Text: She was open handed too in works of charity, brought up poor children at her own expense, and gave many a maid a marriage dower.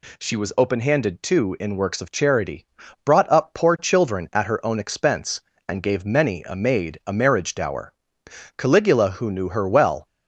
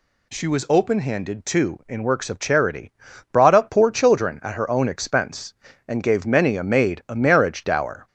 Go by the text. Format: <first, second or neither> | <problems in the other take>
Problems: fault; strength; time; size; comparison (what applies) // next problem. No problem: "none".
second | goes on to say "Caligula who knew her well"; from 8.5 s on; 1.5 s long